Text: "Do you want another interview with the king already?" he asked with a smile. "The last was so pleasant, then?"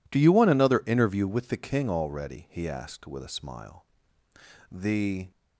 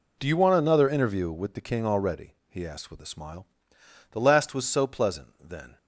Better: second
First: stops before "last was so pleasant then"; at 5.3 s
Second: none

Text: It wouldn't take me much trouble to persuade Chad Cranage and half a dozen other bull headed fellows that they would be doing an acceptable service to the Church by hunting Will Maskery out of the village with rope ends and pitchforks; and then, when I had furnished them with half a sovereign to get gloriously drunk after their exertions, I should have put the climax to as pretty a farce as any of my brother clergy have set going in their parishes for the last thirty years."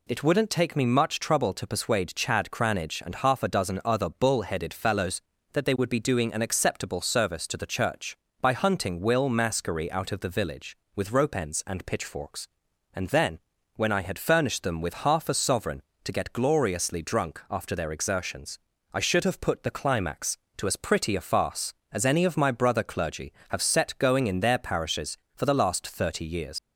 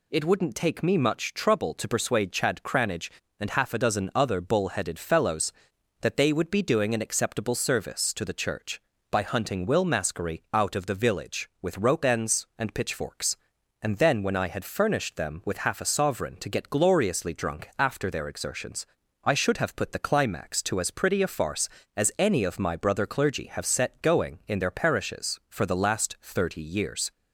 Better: second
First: leaves "years" unfinished; at 26.5 s; 110 ms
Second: none

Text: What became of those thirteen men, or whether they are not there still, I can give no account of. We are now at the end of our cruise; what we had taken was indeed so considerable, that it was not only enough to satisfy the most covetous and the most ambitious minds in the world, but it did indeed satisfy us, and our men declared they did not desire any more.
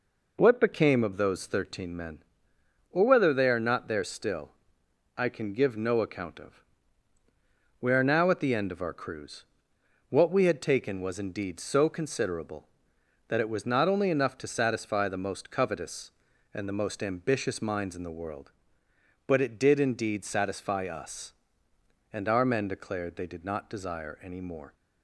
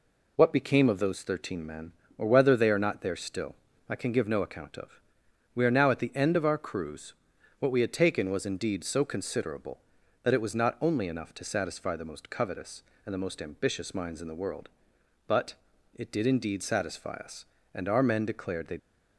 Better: first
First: none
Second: pauses between "but" and "it"; at 15.5 s; 0.40 s long // stops before "did not desire any more"; at 18.7 s

